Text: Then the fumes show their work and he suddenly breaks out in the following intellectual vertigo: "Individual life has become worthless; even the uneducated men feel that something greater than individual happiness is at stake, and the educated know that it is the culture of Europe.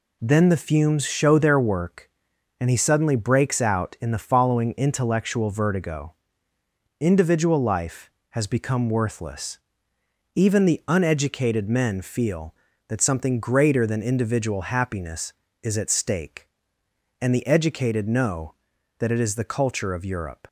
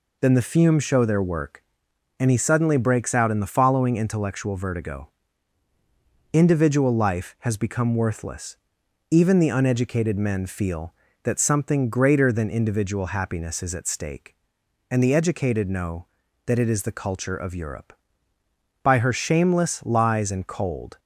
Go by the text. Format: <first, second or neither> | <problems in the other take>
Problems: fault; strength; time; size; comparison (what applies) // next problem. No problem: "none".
first | goes on to say "By her shameless lies and cold"; strong; from 18.8 s on; 2.1 s long